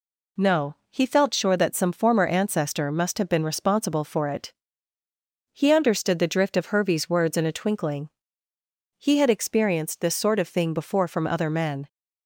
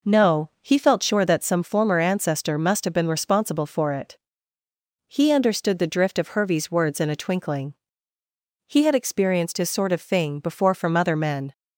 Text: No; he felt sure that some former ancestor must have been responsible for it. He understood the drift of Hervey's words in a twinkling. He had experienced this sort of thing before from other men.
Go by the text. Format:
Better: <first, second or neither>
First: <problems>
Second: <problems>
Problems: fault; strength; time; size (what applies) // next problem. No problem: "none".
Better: first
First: none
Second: says "his" for "this"; at 9.5 s